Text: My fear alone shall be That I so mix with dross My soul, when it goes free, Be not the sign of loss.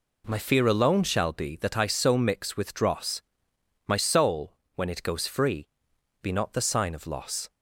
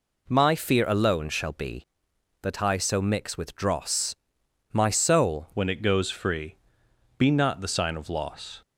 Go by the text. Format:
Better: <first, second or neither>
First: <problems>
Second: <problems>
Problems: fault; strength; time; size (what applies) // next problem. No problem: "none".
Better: first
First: pauses between "dross" and "My"; noticeable; at 3.1 s; 0.66 s long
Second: pauses between "dross" and "My"; noticeable; at 4.1 s; 0.56 s long // changes voice at "when"; from 5.5 s on; 3.1 s long